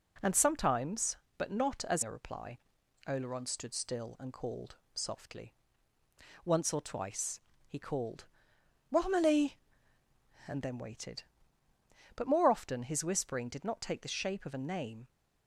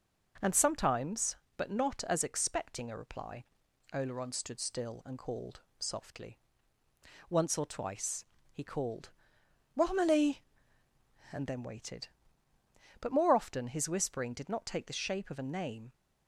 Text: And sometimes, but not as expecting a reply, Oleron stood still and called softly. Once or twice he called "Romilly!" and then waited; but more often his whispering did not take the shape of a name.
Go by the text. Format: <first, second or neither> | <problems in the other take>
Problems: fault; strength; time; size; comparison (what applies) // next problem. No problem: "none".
second | skips "expecting"; at 2.0 s // pauses between "called" and "softly"; slight; at 4.7 s; 0.18 s long; slight in the second // pauses between "twice" and "he"; slight; at 7.4 s; 0.26 s long; slight in the second // pauses between "called" and "Romilly"; noticeable; at 8.2 s; 0.66 s long; noticeable in the second